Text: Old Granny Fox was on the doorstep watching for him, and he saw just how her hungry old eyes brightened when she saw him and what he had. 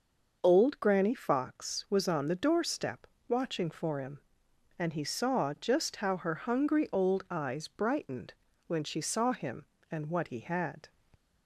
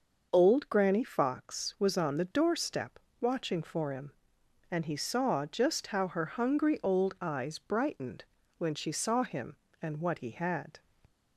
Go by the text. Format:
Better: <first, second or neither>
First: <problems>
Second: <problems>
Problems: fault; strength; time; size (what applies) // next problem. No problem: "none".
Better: neither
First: starts louder than the rest; noticeable; until 1.4 s; 6 dB // pauses between "doorstep" and "watching"; slight; at 3.0 s; 0.22 s long // pauses between "brightened" and "when"; slight; at 8.3 s; 0.32 s long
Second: starts louder than the rest; noticeable; until 1.3 s; 6 dB // pauses between "doorstep" and "watching"; slight; at 2.9 s; 0.22 s long // pauses between "brightened" and "when"; slight; at 8.2 s; 0.32 s long